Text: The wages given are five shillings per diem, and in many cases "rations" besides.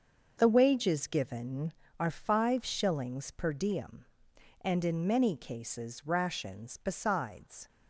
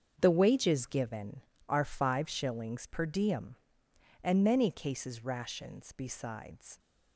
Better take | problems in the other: first | starts louder than the rest; until 1.1 s; 7 dB; also in the first // skips "in"; at 4.4 s

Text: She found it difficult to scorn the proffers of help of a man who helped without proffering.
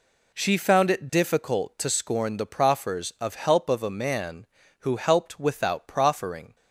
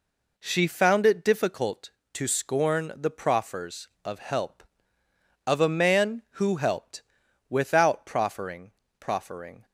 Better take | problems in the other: first | pauses between "helped" and "without"; noticeable; at 7.0 s; 0.48 s long // says "proffering" twice; at 8.9 s

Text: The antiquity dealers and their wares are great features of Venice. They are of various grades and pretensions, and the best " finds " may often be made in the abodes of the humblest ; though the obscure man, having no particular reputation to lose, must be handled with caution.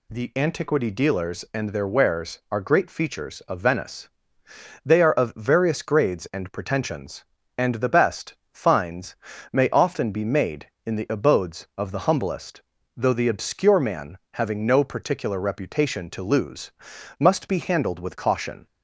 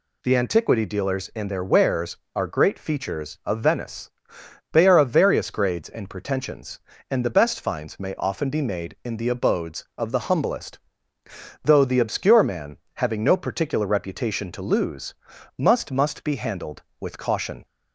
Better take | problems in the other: first | says "must" twice; at 15.9 s

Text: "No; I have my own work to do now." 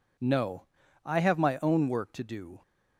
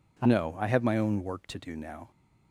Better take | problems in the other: second | stops before "now"; at 2.6 s

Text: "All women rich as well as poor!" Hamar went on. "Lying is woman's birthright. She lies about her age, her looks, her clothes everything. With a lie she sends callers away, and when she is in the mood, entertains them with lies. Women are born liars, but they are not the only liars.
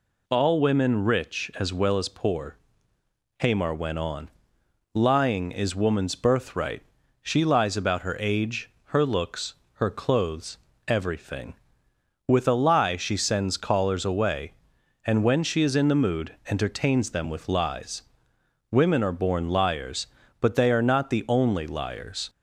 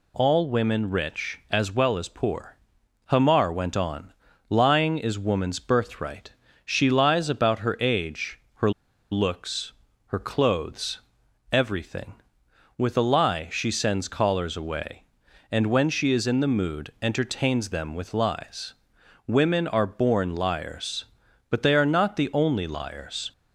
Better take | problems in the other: first | pauses between "her" and "looks"; at 8.7 s; 0.40 s long // pauses between "clothes" and "everything"; noticeable; at 10.9 s; 0.52 s long; slight in the first

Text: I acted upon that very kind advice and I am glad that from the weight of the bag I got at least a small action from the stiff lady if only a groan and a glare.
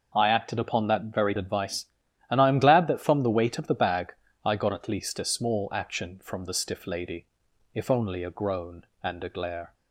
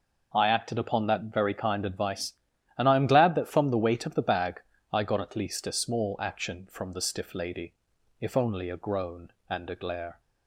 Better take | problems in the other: second | skips "kind"; at 1.3 s // pauses between "bag" and "I"; slight; at 4.1 s; 0.30 s long; slight in the second // pauses between "lady" and "if"; noticeable; at 7.2 s; 0.48 s long; noticeable in the second

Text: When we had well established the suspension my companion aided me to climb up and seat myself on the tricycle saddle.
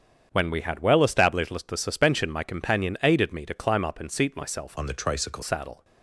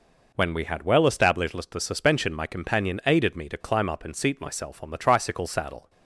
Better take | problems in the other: second | starts louder than the rest; strong; until 1.3 s; 8 dB // changes voice from "on" to "tricycle"; from 4.7 to 5.4 s; 0.7 s long

